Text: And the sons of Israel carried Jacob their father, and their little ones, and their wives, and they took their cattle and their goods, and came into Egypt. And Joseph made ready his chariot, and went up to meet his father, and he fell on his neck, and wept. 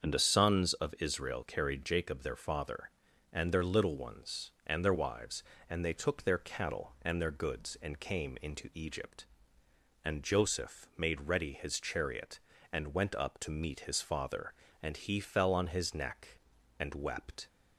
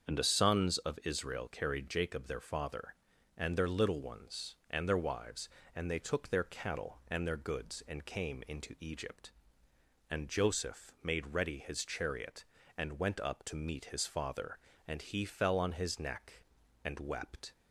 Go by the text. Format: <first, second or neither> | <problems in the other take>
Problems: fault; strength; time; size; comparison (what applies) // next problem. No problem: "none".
neither | starts louder than the rest; the same in both